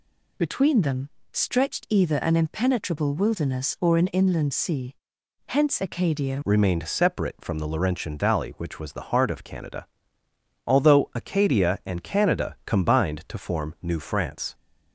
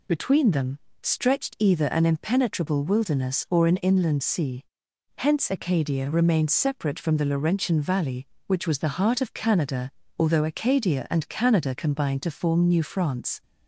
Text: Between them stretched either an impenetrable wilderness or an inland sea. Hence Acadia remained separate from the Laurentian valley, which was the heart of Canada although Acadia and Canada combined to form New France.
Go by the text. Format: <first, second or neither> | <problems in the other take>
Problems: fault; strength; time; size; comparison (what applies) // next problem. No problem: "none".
second | pauses between "them" and "stretched"; slight; at 1.0 s; 0.22 s long; slight in the second // changes voice at "remained"; from 6.4 s on; 8.1 s long // pauses between "Canada" and "although"; noticeable; at 9.8 s; 0.78 s long; slight in the second